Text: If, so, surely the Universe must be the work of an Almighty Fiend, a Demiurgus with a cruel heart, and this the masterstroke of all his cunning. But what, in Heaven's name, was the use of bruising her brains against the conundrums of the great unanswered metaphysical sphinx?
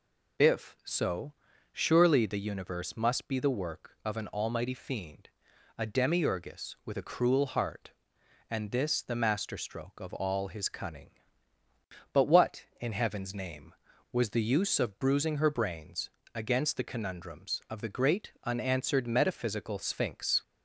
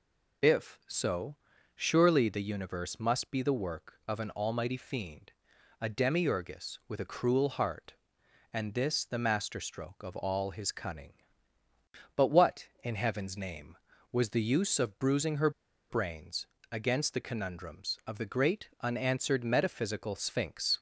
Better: first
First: pauses between "brains" and "against"; slight; at 16.0 s; 0.26 s long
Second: pauses between "her" and "brains"; at 15.4 s; 0.40 s long // pauses between "brains" and "against"; slight; at 16.4 s; 0.26 s long

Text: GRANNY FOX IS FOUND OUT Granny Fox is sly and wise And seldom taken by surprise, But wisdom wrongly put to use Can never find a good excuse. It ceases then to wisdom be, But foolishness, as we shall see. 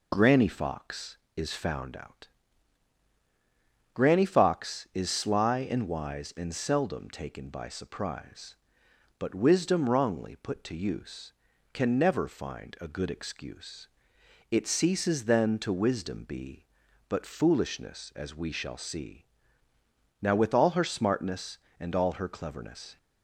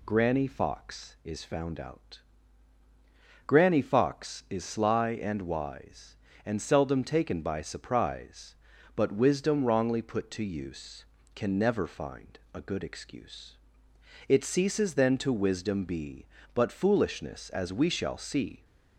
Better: second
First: pauses between "OUT" and "Granny"; strong; at 2.2 s; 1.6 s long // goes on to say "NOW with all her smartness and all her cleverness"; strong; from 20.2 s on; 2.7 s long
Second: pauses between "OUT" and "Granny"; strong; at 2.1 s; 1.2 s long

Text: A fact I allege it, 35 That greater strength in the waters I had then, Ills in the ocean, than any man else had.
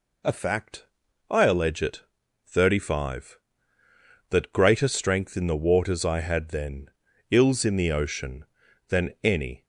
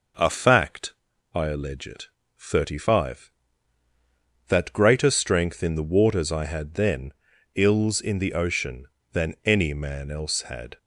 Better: second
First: pauses between "fact" and "I"; noticeable; at 0.8 s; 0.46 s long // stops before "man else had"; at 9.6 s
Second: pauses between "fact" and "I"; at 0.9 s; 0.40 s long

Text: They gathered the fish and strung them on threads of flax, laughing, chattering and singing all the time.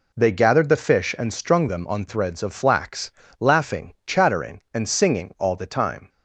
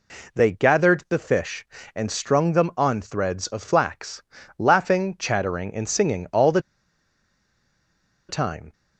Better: first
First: none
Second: pauses between "the" and "time"; strong; at 6.5 s; 1.6 s long

